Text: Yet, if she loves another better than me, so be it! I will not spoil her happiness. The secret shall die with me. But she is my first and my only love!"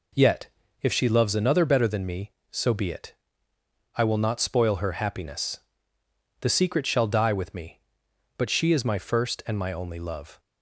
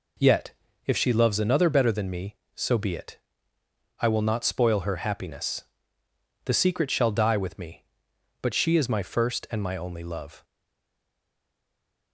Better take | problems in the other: first | stays silent after the last word; noticeable; from 10.4 s on; 1.7 s long

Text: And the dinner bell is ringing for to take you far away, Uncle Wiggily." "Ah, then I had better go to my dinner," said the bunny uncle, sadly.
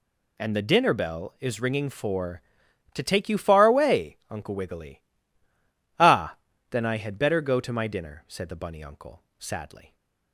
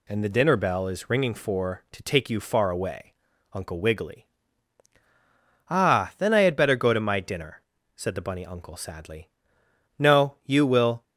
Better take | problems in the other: first | goes on to say "No You will"; noticeable; from 9.9 s on; 1.0 s long

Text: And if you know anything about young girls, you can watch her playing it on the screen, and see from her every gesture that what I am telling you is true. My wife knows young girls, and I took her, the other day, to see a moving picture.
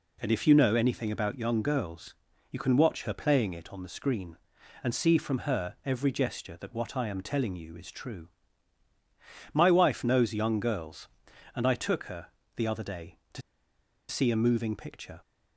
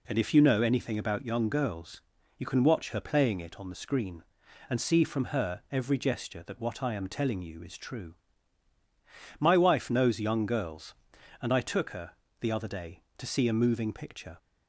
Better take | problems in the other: second | pauses between "to" and "see"; noticeable; at 13.4 s; 0.67 s long

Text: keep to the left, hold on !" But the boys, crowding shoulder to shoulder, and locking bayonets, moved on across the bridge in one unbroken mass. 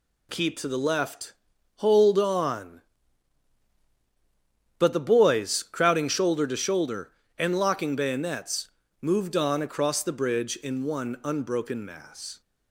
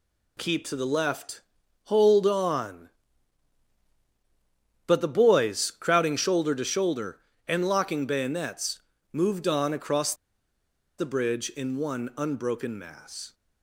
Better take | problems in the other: first | pauses between "across" and "the"; noticeable; at 10.1 s; 0.84 s long

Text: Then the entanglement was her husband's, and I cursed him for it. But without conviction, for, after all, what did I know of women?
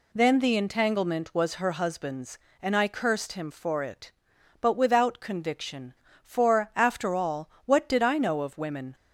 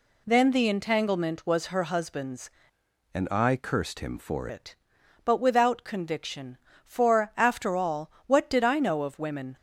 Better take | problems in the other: first | changes voice from "and" to "for"; from 3.1 to 4.4 s; 1.3 s long

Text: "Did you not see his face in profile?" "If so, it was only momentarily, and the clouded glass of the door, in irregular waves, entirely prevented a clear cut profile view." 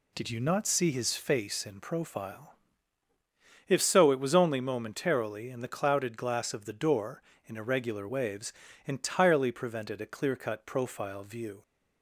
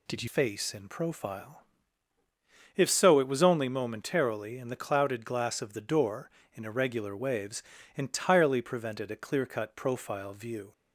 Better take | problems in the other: first | skips "not see his"; at 0.2 s

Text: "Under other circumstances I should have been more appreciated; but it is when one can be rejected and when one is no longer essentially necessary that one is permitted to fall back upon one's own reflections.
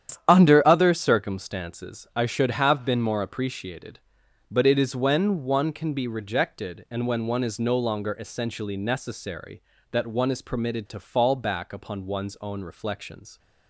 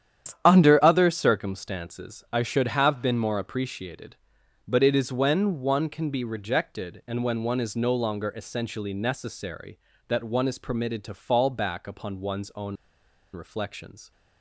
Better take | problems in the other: first | starts louder than the rest; strong; until 1.4 s; 9.5 dB; strong in the first // pauses between "own" and "reflections"; noticeable; at 12.7 s; 0.58 s long

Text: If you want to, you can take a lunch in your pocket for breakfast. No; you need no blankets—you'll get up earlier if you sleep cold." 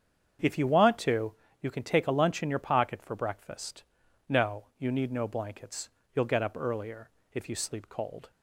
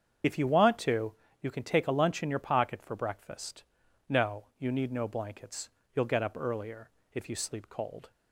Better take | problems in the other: first | loses the start of "If"; at 0.2 s; 50 ms // starts louder than the rest; strong; until 1.5 s; 7.5 dB; strong in the first // pauses between "earlier" and "if"; slight; at 6.9 s; 0.24 s long; slight in the first

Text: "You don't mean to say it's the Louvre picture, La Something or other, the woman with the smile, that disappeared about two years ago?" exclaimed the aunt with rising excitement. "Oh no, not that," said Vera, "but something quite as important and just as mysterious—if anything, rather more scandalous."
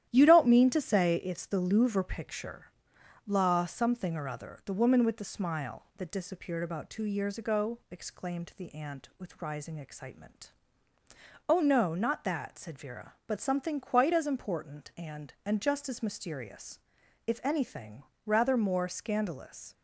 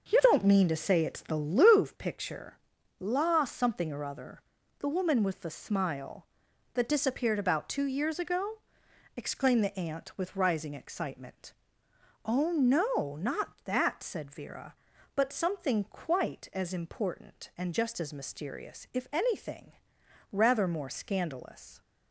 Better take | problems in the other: second | starts louder than the rest; strong; until 1.1 s; 11.5 dB; noticeable in the second // says "and" twice; at 15.4 s

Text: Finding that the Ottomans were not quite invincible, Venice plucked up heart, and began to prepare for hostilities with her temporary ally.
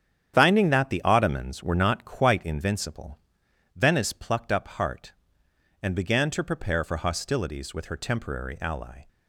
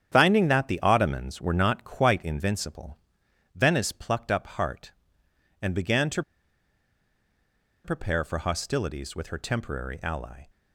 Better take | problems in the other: first | starts louder than the rest; strong; until 1.1 s; 9 dB; strong in the first // pauses between "to" and "prepare"; strong; at 6.2 s; 1.6 s long

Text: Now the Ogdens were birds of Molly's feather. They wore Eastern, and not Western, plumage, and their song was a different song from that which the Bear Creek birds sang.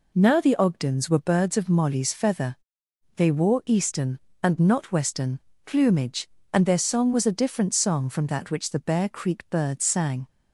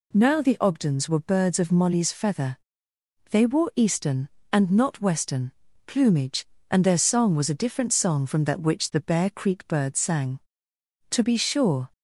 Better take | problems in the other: first | goes on to say "To be sure"; noticeable; from 11.1 s on; 0.80 s long

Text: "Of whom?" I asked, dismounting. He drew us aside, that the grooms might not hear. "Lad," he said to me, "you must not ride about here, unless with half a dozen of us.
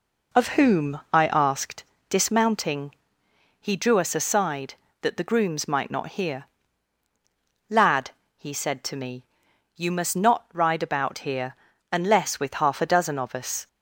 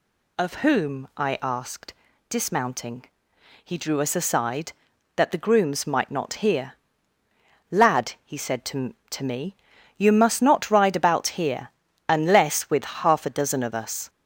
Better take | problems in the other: first | says "to" twice; at 9.1 s

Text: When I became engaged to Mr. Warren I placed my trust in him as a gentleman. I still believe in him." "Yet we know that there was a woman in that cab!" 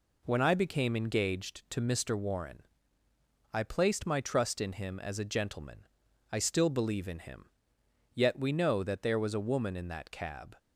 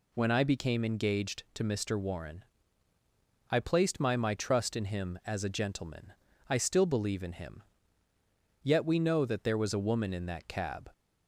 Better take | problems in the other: first | pauses between "Warren" and "I"; at 2.4 s; 1.0 s long; noticeable in the first // says "my" twice; at 4.1 s

